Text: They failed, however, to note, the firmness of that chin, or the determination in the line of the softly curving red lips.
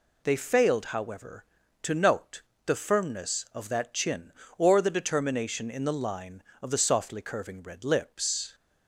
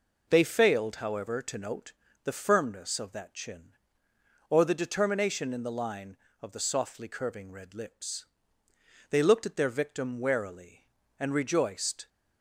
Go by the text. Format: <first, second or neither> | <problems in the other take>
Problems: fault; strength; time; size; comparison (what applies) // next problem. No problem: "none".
first | goes on to say "They looked at their victim warily and rejoiced"; strong; from 9.1 s on; 2.9 s long